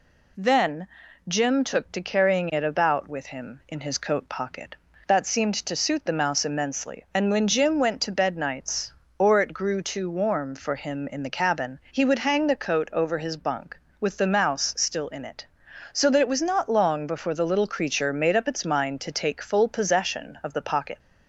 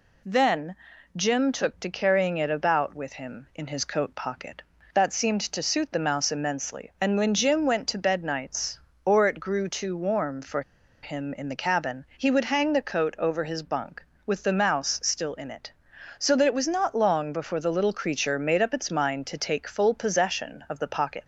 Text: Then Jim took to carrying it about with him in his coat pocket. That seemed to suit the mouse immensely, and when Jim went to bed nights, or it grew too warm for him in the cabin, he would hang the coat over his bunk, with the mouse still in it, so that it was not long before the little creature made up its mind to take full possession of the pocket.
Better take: first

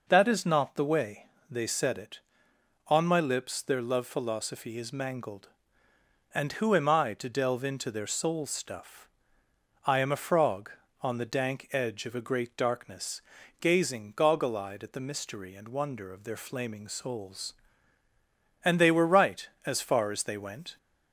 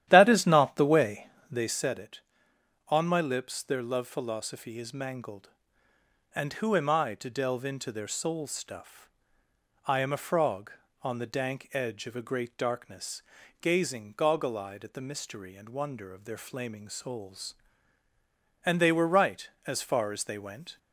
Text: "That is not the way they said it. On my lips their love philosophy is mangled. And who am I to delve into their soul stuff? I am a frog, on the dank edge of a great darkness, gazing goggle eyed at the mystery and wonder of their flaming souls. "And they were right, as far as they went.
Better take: first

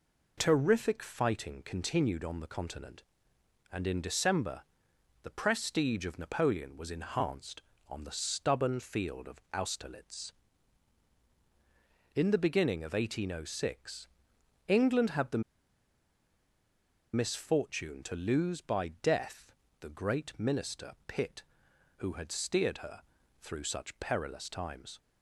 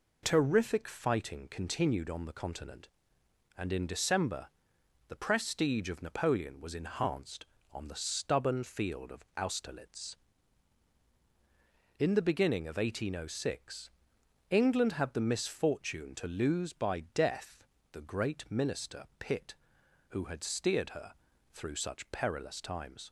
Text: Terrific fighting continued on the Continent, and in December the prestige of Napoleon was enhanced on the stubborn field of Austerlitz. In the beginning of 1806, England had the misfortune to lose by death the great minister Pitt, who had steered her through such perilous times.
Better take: second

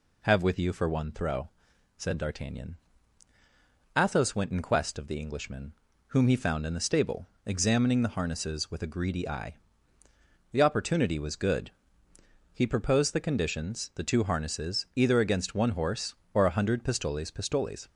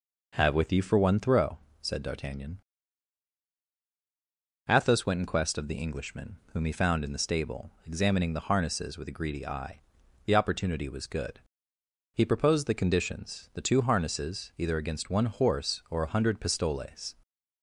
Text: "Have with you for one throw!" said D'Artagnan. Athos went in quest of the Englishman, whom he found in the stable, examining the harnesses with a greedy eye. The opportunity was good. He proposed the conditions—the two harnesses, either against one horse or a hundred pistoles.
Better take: second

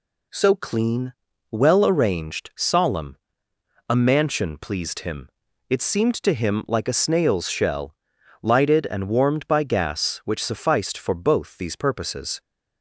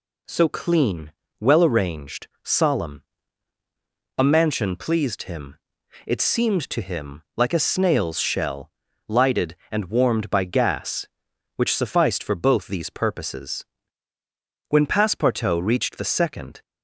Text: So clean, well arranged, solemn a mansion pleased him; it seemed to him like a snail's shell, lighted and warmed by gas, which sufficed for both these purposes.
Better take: first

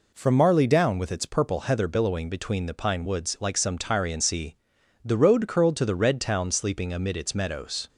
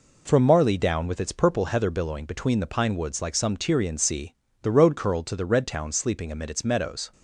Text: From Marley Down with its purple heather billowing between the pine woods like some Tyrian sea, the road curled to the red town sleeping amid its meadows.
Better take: neither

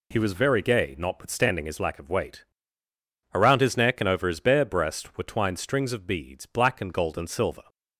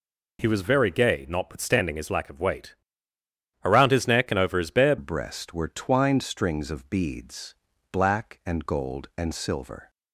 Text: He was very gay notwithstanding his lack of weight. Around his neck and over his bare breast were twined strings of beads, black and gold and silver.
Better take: first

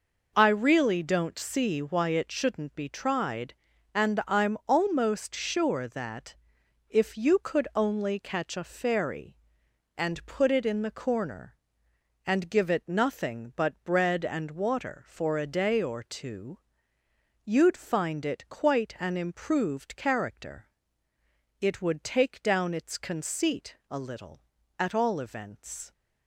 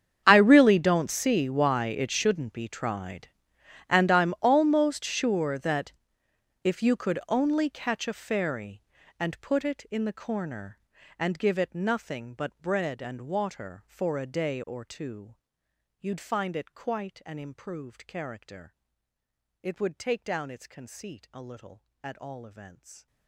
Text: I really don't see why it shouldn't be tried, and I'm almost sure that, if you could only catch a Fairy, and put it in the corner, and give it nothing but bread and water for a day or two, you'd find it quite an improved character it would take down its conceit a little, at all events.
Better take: first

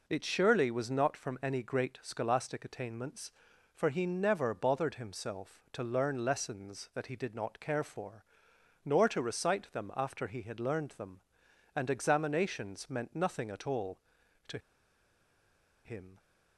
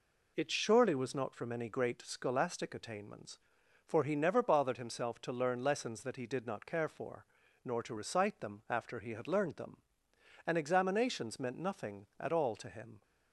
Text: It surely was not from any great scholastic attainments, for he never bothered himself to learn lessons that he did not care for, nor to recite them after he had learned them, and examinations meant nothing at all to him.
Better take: second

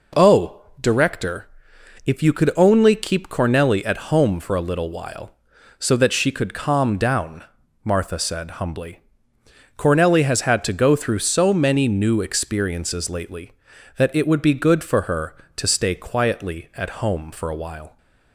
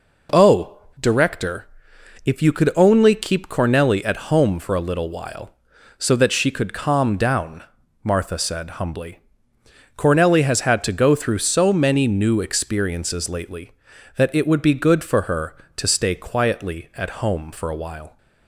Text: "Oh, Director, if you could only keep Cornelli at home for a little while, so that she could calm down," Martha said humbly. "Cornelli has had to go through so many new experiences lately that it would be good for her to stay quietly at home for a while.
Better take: neither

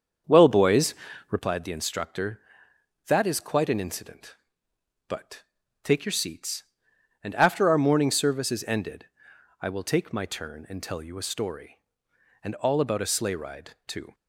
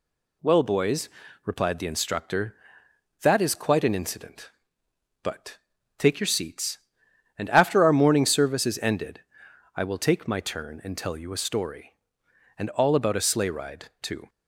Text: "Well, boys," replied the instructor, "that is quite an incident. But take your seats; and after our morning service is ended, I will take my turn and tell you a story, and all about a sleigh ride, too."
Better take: second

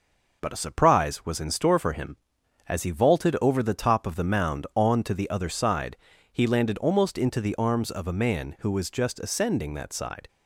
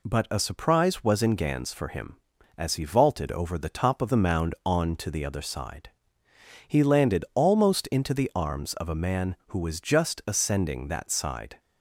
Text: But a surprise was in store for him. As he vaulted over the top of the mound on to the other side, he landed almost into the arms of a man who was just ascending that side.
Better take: first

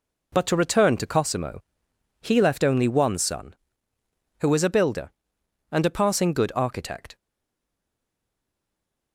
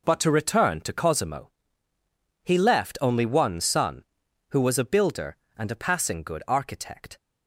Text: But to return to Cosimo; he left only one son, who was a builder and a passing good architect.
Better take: second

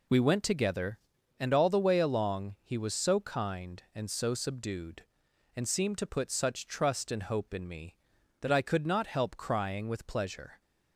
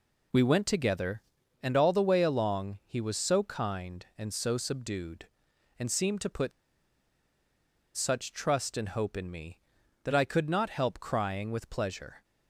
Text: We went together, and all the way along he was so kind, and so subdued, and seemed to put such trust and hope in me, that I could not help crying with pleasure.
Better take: first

